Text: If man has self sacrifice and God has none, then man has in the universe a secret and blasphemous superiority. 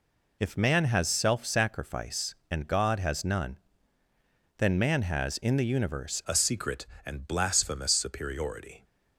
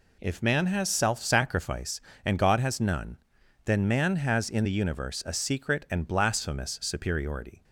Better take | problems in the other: second | changes voice at "a"; from 6.2 s on; 2.6 s long

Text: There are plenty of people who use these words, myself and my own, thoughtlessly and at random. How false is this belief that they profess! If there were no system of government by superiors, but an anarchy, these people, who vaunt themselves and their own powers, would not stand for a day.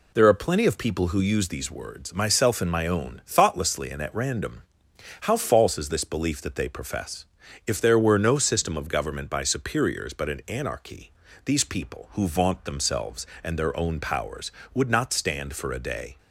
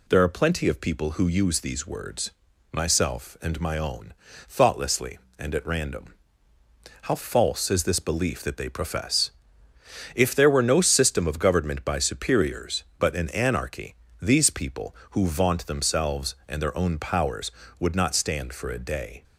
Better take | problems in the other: neither | none

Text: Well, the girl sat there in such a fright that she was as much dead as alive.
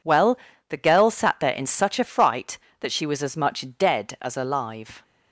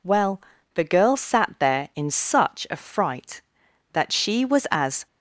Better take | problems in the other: first | stops before "much dead as alive"; at 5.0 s

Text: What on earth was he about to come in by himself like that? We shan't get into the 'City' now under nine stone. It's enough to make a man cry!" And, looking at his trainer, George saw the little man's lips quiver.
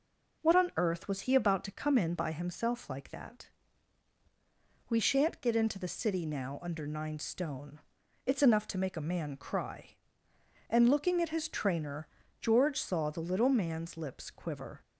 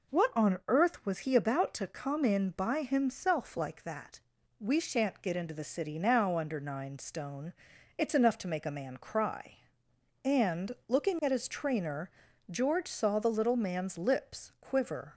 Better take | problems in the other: neither | none

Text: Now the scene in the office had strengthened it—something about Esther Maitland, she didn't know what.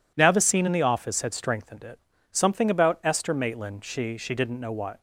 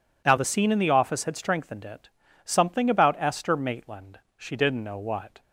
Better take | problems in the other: second | says "she" twice; at 4.1 s

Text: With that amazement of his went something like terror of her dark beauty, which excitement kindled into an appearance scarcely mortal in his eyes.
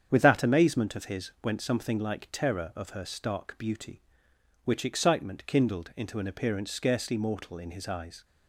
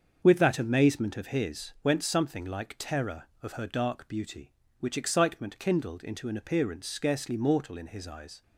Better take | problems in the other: second | starts louder than the rest; strong; until 1.1 s; 8 dB; also in the second // says "stark" for "dark"; at 3.0 s

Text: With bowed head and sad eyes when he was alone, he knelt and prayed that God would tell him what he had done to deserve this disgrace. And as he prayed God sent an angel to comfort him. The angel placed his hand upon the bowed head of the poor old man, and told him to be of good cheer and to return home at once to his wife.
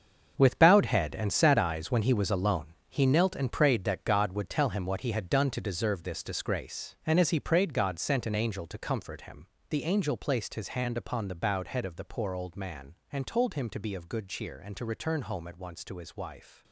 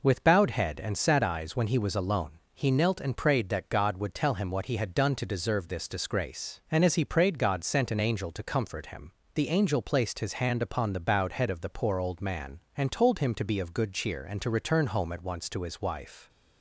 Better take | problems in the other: second | gets quieter; strong; throughout; 11.5 dB

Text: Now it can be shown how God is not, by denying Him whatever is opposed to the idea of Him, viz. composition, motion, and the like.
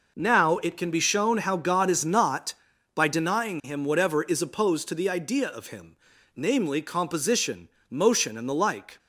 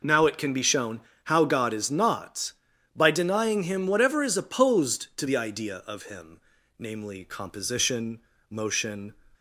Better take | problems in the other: first | pauses between "shown" and "how"; slight; at 0.9 s; 0.26 s long // stops before "and the like"; at 9.3 s

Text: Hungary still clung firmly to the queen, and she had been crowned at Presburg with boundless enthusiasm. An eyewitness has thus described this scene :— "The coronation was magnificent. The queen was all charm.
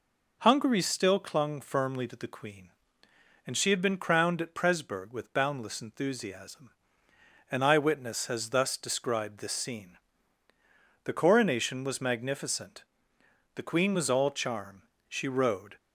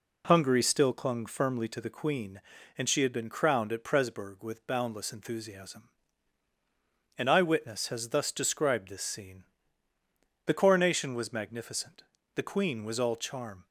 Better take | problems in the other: second | goes on to say "She rode"; noticeable; from 15.0 s on; 0.68 s long

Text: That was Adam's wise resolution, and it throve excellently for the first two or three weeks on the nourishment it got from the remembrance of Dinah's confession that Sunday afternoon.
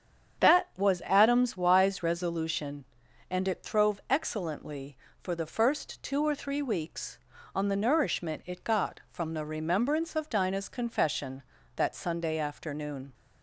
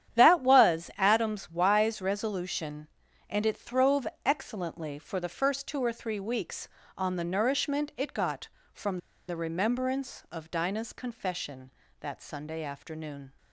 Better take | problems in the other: first | starts louder than the rest; strong; until 1.2 s; 10 dB; strong in the first // pauses between "throve" and "excellently"; slight; at 4.0 s; 0.18 s long // pauses between "from" and "the"; slight; at 8.9 s; 0.30 s long

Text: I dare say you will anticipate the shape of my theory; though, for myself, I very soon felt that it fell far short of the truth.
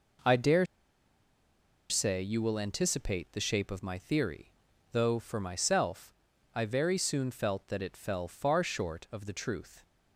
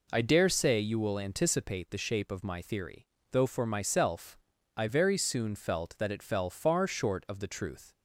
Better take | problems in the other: second | pauses between "dare" and "say"; at 0.6 s; 1.2 s long

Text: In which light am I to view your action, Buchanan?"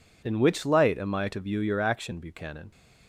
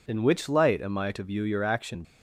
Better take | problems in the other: first | stops before "Buchanan"; at 2.0 s

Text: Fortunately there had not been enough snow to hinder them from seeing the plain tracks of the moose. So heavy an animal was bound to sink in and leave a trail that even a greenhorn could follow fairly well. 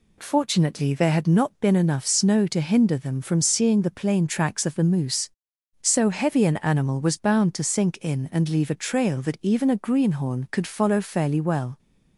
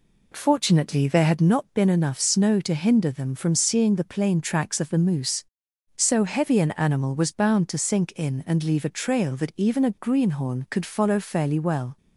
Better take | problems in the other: first | starts louder than the rest; slight; until 1.5 s; 3 dB

